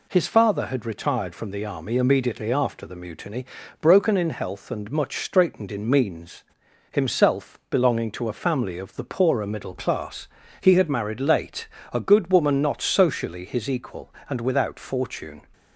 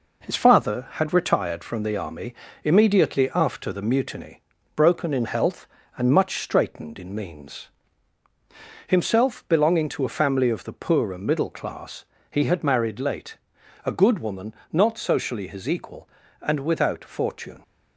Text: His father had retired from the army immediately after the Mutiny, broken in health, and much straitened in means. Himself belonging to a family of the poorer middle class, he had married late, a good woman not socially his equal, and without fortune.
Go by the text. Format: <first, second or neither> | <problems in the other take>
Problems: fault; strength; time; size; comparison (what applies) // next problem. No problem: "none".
first | gets quieter; noticeable; throughout; 5 dB // pauses between "army" and "immediately"; slight; at 2.3 s; 0.30 s long // pauses between "woman" and "not"; slight; at 14.5 s; 0.16 s long